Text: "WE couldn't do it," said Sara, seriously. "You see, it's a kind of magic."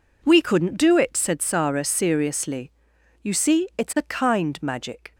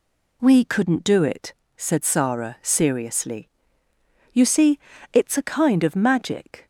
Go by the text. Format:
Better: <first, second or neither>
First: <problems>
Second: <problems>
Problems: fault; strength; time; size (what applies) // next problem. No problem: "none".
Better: second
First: skips "of"; at 4.5 s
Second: none